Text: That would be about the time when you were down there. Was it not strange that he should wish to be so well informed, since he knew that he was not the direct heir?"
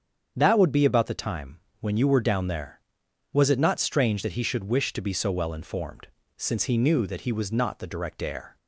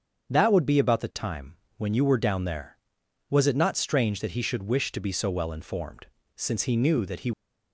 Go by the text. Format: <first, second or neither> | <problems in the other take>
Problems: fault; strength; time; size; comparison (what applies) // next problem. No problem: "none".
first | starts louder than the rest; strong; until 1.3 s; 7.5 dB; strong in the first // pauses between "time" and "when"; slight; at 1.5 s; 0.22 s long; slight in the first // stops before "was not the direct heir"; at 7.3 s